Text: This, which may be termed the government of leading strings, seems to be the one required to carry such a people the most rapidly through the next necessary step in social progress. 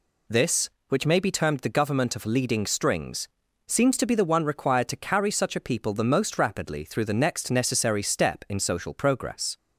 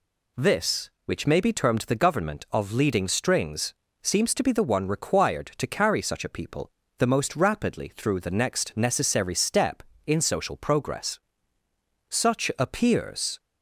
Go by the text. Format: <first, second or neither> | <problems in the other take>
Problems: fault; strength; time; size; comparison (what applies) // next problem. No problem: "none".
first | pauses between "people" and "the"; slight; at 6.6 s; 0.28 s long // goes on to say "Such appears"; noticeable; from 12.0 s on; 1.3 s long